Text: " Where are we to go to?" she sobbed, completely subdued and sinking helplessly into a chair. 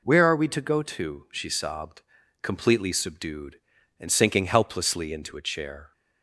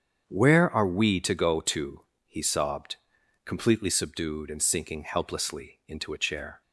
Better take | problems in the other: first | starts louder than the rest; strong; until 1.3 s; 8.5 dB // says "he" for "she"; at 2.2 s

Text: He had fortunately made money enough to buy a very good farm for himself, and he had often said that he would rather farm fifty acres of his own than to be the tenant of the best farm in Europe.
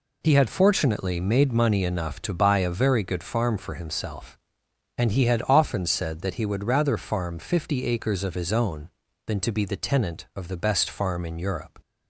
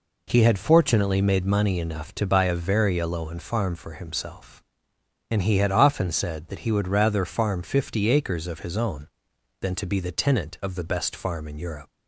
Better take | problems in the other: first | says "aloan" for "good"; at 2.9 s

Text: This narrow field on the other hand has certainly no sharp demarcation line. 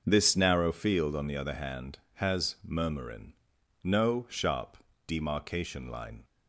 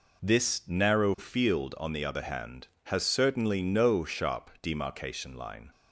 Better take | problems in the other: second | says "murmurin" for "certainly"; at 2.6 s // pauses between "sharp" and "demarcation"; slight; at 4.7 s; 0.31 s long

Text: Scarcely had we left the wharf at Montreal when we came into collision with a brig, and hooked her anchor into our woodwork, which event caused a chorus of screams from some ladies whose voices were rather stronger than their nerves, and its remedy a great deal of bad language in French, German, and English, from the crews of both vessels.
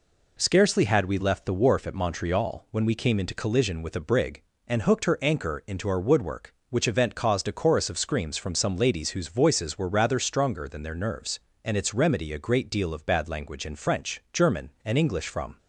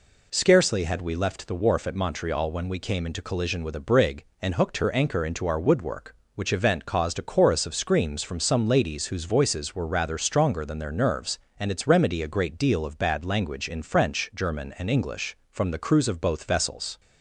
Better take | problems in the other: second | stops before "the crews of both vessels"; at 15.5 s

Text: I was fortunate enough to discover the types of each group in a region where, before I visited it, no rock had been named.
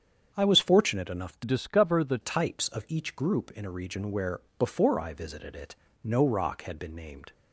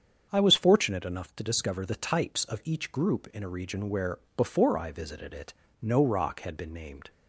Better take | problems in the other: second | starts louder than the rest; strong; until 1.3 s; 7.5 dB; strong in the second // changes voice from "discover" to "the"; from 1.4 to 2.1 s; 0.7 s long

